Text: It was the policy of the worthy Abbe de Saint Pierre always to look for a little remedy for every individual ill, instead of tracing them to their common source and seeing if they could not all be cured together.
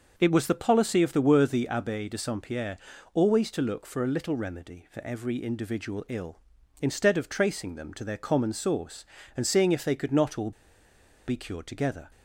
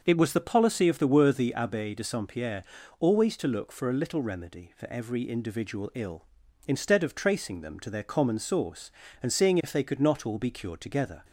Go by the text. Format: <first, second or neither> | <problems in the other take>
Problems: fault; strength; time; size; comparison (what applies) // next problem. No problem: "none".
second | starts louder than the rest; until 1.1 s; 6.5 dB; also in the second // pauses between "Pierre" and "always"; slight; at 2.7 s; 0.34 s long; slight in the second // pauses between "all" and "be"; noticeable; at 10.5 s; 0.77 s long